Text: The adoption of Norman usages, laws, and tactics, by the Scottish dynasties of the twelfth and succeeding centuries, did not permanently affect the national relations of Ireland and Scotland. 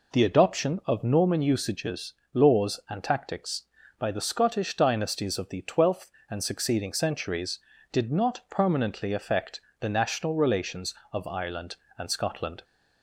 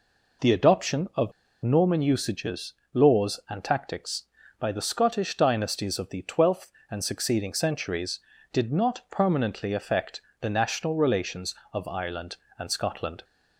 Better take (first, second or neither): first